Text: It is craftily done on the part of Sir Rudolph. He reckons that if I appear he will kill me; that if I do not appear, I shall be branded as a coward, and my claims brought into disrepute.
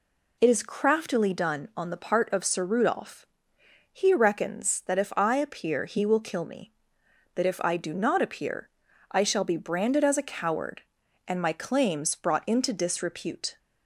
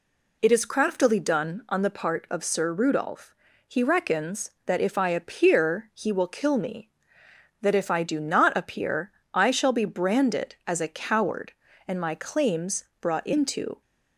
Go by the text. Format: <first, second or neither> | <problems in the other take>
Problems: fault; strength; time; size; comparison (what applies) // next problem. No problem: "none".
first | pauses between "claims" and "brought"; slight; at 12.8 s; 0.16 s long // stops before "disrepute"; at 13.8 s